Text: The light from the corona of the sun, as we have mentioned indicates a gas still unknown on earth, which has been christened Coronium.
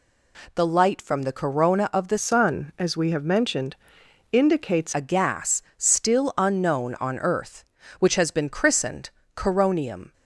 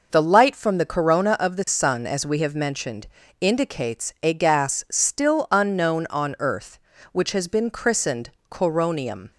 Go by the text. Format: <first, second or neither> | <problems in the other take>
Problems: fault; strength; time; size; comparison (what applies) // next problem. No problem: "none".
second | changes voice from "sun" to "indicates"; from 2.1 to 4.9 s; 2.8 s long // pauses between "mentioned" and "indicates"; noticeable; at 3.7 s; 0.58 s long; slight in the second // pauses between "christened" and "Coronium"; slight; at 9.1 s; 0.26 s long; slight in the second